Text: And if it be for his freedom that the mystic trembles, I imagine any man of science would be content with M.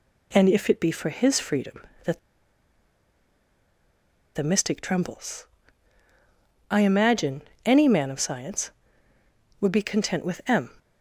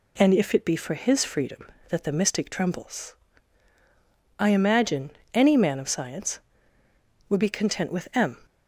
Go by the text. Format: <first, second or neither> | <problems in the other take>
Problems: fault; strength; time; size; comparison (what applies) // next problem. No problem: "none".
second | pauses between "that" and "the"; strong; at 2.1 s; 2.1 s long // pauses between "imagine" and "any"; slight; at 7.4 s; 0.24 s long; slight in the second